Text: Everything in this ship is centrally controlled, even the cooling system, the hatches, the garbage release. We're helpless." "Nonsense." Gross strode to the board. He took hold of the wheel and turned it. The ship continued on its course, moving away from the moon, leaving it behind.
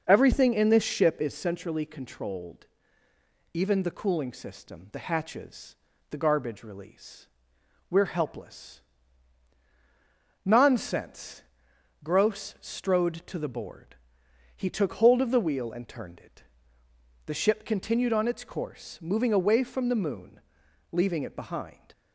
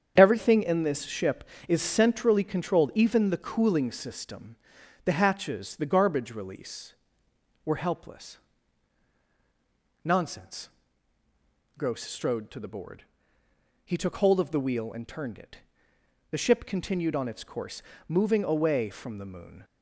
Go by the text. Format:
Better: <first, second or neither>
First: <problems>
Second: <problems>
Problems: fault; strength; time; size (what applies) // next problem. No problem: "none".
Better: first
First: starts louder than the rest; noticeable; until 1.0 s; 6 dB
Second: starts louder than the rest; strong; until 1.1 s; 8 dB // stops before "leaving it behind"; at 19.6 s